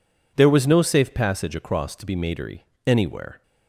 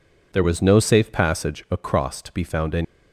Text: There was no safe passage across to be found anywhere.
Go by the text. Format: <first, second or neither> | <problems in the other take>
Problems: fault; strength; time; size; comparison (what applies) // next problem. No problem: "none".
second | says "matery" for "found"; at 2.1 s